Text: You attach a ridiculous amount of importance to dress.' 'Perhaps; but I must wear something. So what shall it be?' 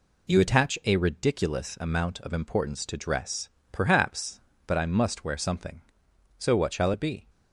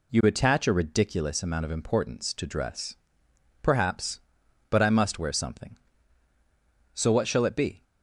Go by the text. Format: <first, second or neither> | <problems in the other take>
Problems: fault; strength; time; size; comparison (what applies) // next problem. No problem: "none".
neither | none